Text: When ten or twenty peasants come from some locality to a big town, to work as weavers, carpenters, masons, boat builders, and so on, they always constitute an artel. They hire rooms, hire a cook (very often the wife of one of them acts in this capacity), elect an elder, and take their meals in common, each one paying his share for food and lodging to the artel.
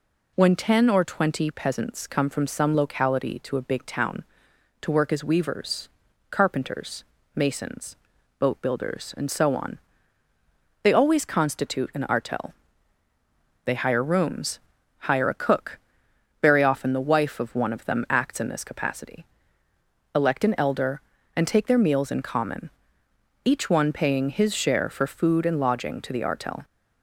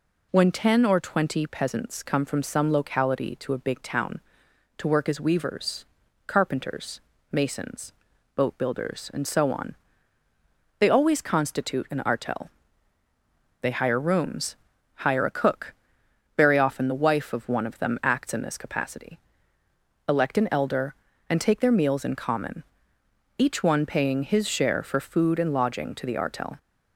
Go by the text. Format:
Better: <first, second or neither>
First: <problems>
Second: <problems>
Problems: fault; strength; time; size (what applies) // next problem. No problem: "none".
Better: neither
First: none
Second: none